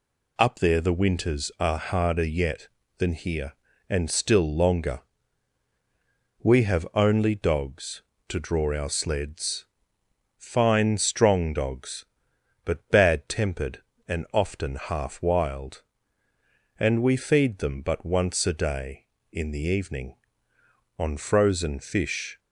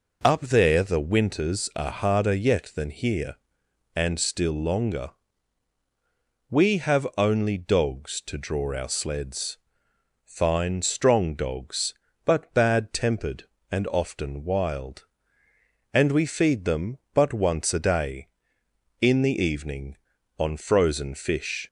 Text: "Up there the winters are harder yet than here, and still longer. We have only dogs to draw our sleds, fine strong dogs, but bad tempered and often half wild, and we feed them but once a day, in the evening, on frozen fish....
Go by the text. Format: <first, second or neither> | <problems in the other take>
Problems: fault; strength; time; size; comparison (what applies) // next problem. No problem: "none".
first | skips "half"; at 14.4 s